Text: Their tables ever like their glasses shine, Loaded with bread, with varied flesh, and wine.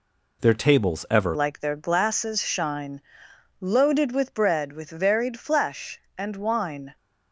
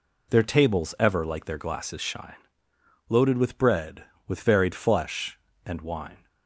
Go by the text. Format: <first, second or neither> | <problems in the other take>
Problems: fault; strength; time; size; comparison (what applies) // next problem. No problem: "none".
second | changes voice at "like"; from 1.3 s on; 5.6 s long